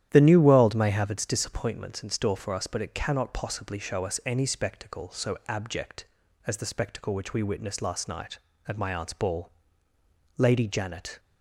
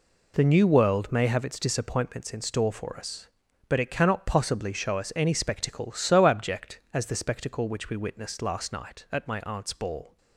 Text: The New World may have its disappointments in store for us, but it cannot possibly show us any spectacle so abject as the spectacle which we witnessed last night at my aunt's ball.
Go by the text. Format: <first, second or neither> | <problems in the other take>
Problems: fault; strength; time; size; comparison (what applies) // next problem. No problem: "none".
second | starts louder than the rest; strong; until 1.1 s; 11 dB // goes on to say "Lady Janet"; noticeable; from 10.3 s on; 0.84 s long